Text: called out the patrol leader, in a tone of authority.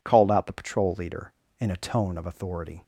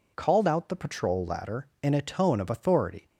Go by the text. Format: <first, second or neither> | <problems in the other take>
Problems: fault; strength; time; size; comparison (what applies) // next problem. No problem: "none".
first | says "ladder" for "leader"; at 1.2 s